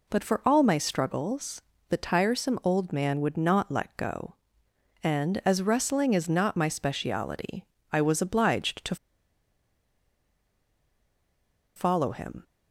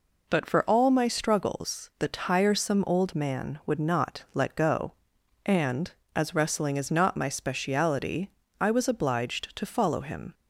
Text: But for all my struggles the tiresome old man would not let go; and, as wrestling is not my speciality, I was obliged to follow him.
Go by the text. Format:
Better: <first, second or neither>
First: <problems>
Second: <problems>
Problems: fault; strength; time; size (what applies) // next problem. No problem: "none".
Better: second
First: pauses between "struggles" and "the"; slight; at 1.6 s; 0.28 s long // pauses between "to" and "follow"; strong; at 8.9 s; 2.8 s long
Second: none